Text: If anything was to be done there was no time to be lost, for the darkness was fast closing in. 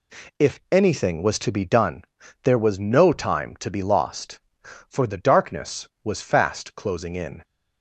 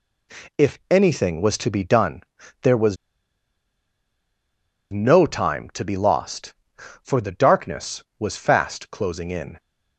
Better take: first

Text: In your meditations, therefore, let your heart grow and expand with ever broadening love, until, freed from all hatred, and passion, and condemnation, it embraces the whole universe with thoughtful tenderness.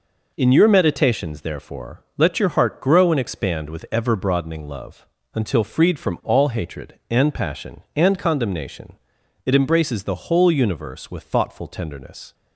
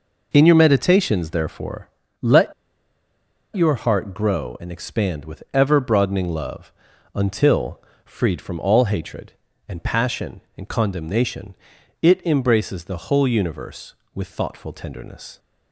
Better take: first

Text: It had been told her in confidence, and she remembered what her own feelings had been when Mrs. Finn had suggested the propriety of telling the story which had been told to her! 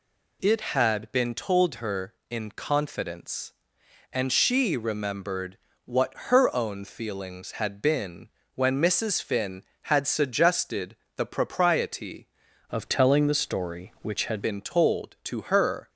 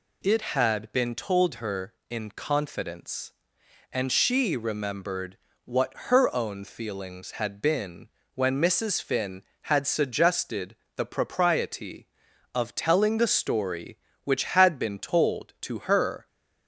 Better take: second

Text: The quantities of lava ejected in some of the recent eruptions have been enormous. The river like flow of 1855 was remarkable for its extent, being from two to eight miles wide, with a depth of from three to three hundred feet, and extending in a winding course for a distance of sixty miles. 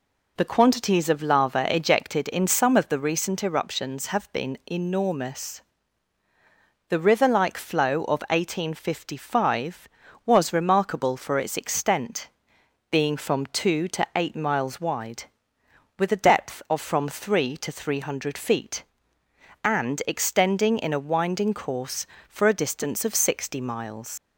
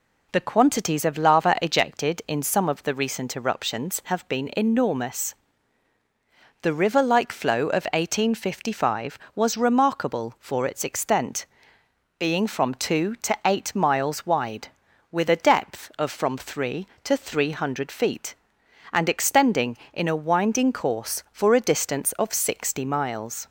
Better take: second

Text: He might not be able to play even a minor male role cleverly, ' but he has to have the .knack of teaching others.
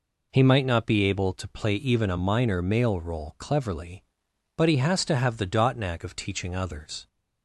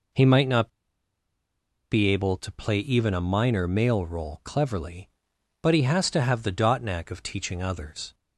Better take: first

